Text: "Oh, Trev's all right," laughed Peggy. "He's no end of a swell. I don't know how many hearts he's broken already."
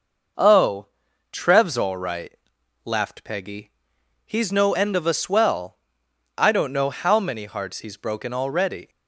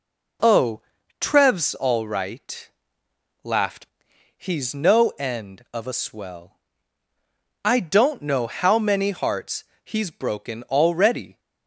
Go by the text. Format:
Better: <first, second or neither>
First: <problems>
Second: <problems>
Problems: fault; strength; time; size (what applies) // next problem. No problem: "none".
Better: first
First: none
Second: skips "Peggy"; at 4.1 s // pauses between "hearts" and "he's"; slight; at 9.6 s; 0.20 s long